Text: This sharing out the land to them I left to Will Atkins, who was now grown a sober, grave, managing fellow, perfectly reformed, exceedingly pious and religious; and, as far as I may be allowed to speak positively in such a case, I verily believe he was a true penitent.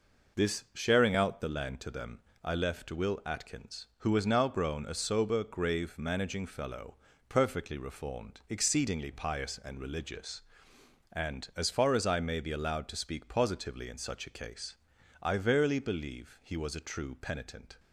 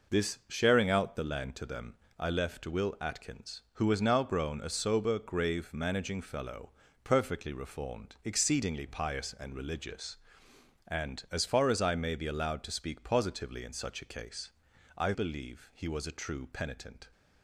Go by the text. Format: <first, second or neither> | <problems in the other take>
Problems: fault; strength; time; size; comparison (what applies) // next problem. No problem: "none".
first | pauses between "them" and "I"; slight; at 1.9 s; 0.24 s long; slight in the first // skips "verily"; at 15.1 s